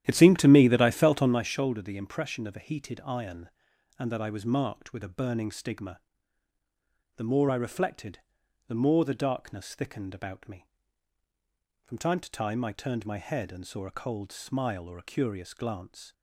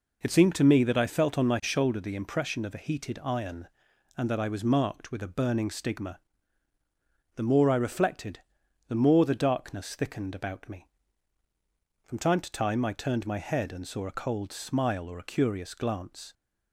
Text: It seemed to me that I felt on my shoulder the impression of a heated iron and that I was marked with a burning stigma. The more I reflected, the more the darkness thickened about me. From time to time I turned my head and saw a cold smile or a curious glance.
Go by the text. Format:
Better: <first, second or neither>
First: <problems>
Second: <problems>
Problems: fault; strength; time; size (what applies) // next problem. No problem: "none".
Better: second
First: starts louder than the rest; strong; until 1.5 s; 11.5 dB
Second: none